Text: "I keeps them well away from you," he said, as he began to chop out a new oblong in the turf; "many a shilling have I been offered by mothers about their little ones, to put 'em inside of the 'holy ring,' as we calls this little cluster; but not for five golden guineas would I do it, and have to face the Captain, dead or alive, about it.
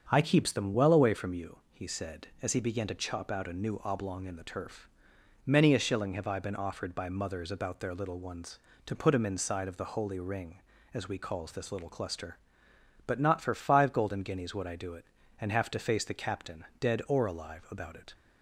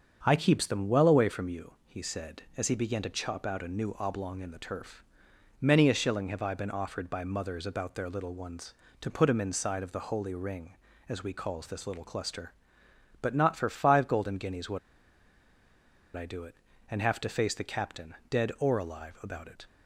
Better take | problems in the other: first | starts louder than the rest; until 1.2 s; 7 dB; also in the first // pauses between "would" and "I"; strong; at 14.7 s; 1.3 s long

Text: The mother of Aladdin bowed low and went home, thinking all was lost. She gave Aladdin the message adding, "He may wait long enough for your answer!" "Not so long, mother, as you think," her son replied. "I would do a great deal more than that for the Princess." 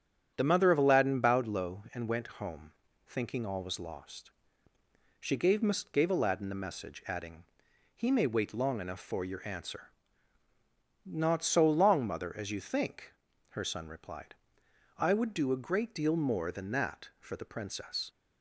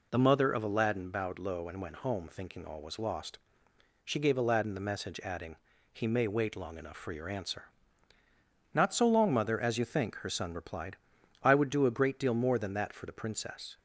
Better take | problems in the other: second | starts louder than the rest; strong; until 1.3 s; 8 dB // says "gave" twice; at 5.9 s

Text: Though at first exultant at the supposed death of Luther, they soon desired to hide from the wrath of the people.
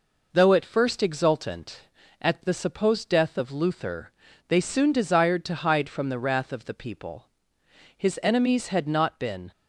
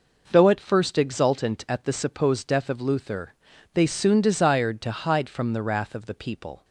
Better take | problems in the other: second | goes on to say "His enemies had not been"; from 7.9 s on; 1.5 s long

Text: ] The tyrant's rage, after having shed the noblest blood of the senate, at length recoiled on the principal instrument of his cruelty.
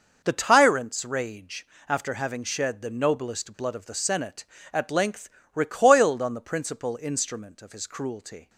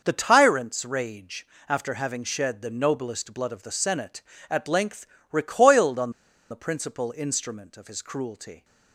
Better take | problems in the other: first | pauses between "length" and "recoiled"; slight; at 5.0 s; 0.24 s long; slight in the first // pauses between "on" and "the"; at 6.1 s; 0.40 s long

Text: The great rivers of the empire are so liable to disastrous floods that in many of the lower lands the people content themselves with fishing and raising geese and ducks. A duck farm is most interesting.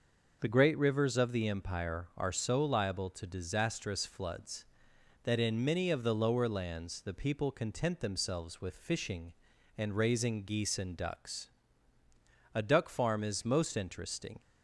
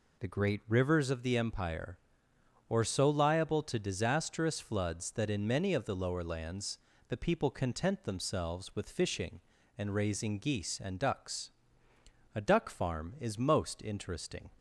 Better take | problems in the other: first | says "or" for "are"; at 2.6 s // pauses between "lands" and "the"; slight; at 6.7 s; 0.30 s long

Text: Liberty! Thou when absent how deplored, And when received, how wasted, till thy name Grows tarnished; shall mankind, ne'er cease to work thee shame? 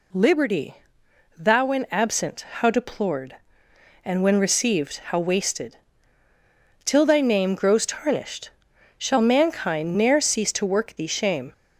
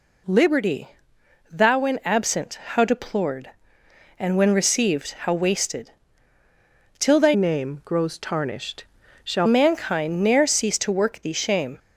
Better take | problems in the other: first | changes voice from "name" to "shall"; from 7.3 to 9.4 s; 2.1 s long

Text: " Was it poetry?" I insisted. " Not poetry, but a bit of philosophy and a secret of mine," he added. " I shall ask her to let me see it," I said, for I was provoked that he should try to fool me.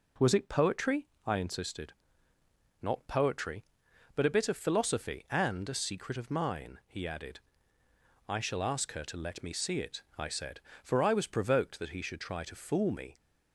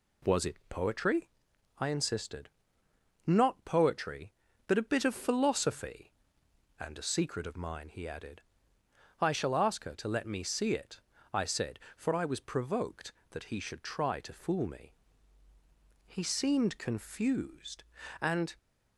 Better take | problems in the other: first | goes on to say "He seemed confused and"; strong; from 16.0 s on; 2.4 s long

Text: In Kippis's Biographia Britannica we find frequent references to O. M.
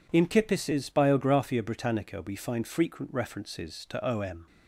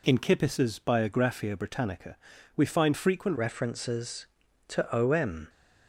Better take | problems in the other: first | pauses between "Britannica" and "we"; at 2.1 s; 0.40 s long // changes voice at "references"; from 3.3 s on; 2.1 s long

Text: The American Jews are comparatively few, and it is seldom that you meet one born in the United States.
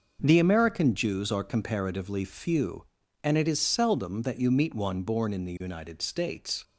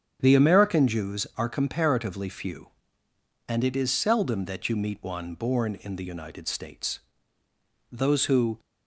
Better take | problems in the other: first | starts louder than the rest; strong; until 1.2 s; 8 dB // goes on to say "Those who"; noticeable; from 7.8 s on; 0.70 s long

